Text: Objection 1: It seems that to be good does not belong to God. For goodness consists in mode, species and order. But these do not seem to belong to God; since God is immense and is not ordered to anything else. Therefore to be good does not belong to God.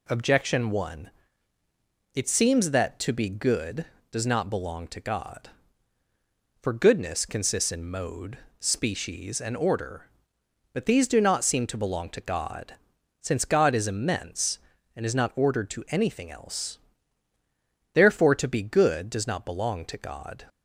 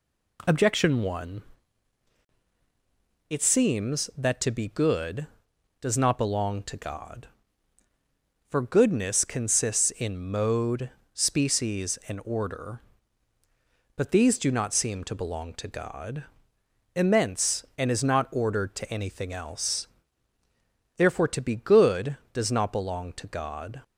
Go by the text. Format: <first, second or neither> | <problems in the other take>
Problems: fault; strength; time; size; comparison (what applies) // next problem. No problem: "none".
first | skips "since God is"; at 16.5 s